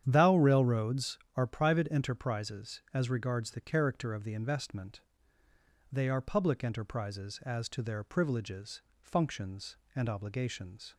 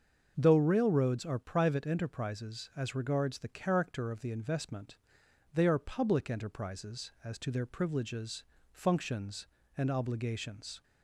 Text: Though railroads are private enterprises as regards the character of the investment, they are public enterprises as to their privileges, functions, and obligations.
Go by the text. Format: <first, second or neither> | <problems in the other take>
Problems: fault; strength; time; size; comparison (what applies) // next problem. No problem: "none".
second | starts louder than the rest; strong; until 1.0 s; 9.5 dB; also in the second // says "Thou" for "Though"; at 0.0 s